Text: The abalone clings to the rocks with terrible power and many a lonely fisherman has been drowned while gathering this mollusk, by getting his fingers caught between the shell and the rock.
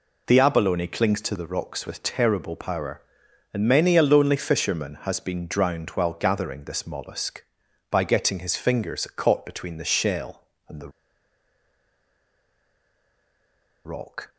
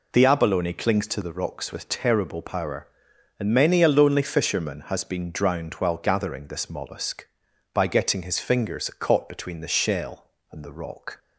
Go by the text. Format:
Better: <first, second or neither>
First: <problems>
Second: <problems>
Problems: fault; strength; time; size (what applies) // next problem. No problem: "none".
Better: second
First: pauses between "the" and "rock"; strong; at 10.8 s; 2.9 s long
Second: none